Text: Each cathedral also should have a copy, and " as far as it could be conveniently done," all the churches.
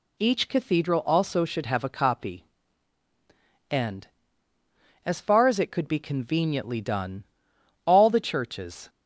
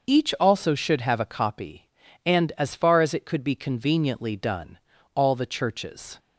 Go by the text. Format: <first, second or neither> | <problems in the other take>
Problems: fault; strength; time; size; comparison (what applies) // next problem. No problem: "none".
first | starts louder than the rest; until 1.1 s; 6.5 dB // skips "cathedral"; at 0.3 s